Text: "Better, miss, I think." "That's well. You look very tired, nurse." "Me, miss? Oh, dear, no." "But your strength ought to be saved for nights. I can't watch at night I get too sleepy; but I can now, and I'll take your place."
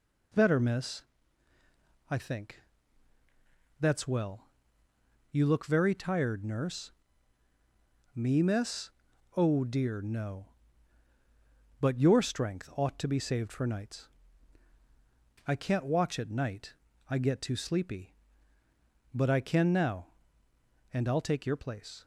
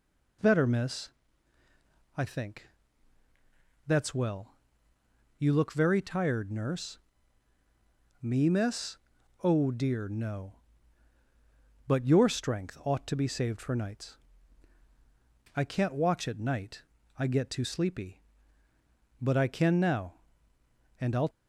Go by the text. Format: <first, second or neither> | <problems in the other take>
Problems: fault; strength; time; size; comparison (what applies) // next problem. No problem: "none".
first | pauses between "night" and "I"; slight; at 16.8 s; 0.34 s long; slight in the first // stops before "take your place"; at 21.3 s